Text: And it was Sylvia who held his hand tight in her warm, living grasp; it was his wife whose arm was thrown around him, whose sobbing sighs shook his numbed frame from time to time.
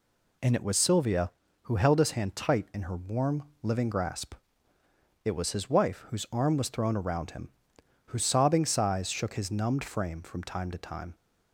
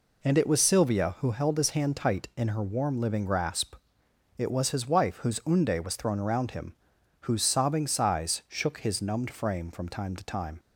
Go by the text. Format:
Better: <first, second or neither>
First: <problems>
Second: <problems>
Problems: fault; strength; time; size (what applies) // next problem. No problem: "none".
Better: first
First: none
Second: says "unde" for "arm"; at 5.4 s